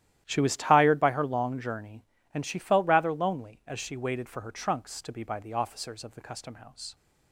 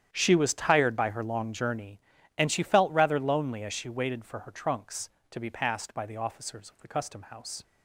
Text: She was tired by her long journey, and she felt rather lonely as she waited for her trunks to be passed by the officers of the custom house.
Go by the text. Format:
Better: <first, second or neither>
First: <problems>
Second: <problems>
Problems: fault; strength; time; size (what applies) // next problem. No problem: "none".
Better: second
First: starts louder than the rest; strong; until 1.2 s; 12.5 dB // skips "passed"; at 5.2 s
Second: starts louder than the rest; strong; until 1.1 s; 10 dB